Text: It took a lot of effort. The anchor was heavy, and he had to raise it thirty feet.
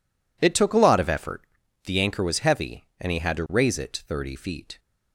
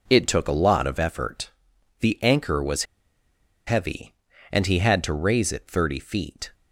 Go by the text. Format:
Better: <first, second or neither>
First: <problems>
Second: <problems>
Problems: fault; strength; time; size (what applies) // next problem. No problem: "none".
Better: first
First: none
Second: pauses between "was" and "heavy"; noticeable; at 2.8 s; 0.82 s long